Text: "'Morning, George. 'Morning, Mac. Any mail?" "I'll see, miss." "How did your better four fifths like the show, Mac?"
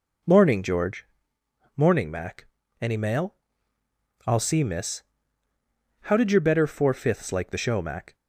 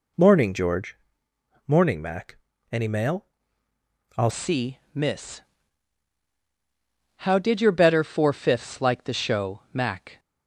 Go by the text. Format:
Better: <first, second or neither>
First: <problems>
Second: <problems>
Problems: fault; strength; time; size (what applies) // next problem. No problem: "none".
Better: first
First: none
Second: changes voice at "see"; from 4.2 s on; 5.9 s long